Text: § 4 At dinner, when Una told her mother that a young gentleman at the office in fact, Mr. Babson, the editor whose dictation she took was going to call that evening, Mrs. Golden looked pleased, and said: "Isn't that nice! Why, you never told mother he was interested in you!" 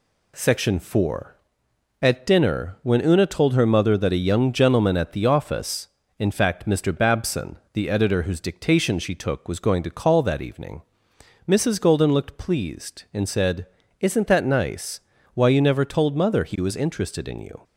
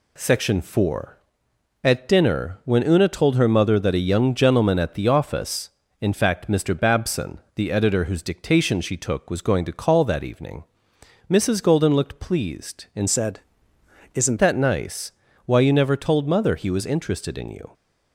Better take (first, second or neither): first